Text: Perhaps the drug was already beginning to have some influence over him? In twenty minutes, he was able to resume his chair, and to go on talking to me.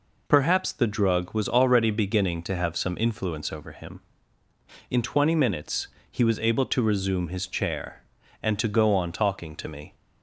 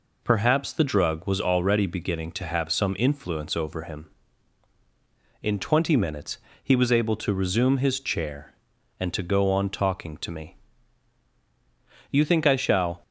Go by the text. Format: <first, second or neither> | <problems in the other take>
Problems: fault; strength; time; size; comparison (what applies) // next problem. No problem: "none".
first | goes on to say "You think I shall"; noticeable; from 12.1 s on; 0.92 s long